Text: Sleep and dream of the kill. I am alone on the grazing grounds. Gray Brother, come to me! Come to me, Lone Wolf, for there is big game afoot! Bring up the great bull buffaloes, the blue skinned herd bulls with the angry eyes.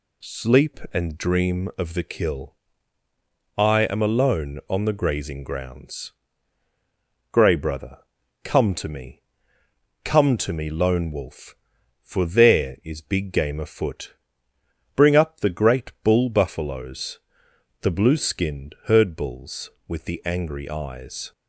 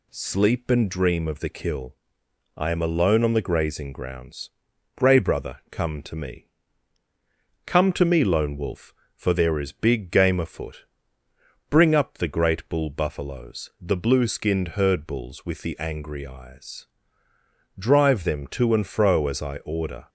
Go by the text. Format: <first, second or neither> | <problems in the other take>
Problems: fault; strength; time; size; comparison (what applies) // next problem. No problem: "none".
first | goes on to say "Drive them to and fro as I order"; strong; from 17.7 s on; 2.3 s long